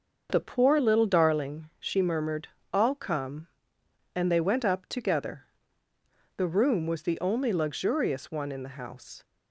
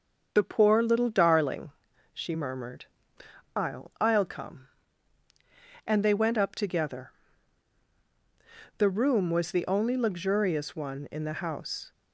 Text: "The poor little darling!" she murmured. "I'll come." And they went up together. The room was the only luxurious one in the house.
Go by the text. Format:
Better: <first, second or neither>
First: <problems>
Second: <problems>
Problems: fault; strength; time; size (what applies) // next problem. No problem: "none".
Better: first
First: starts louder than the rest; until 1.3 s; 6.5 dB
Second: starts louder than the rest; until 1.3 s; 6.5 dB // says "I'll" twice; at 3.9 s